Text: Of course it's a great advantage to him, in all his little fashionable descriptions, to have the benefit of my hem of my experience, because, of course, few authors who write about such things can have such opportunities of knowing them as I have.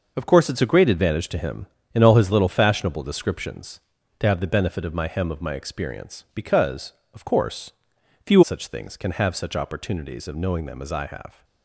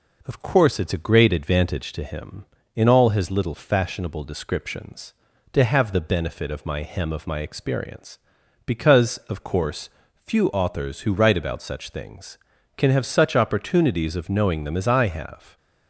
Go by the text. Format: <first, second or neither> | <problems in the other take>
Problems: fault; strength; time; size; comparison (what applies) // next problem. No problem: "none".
second | skips "authors who write about"; at 8.4 s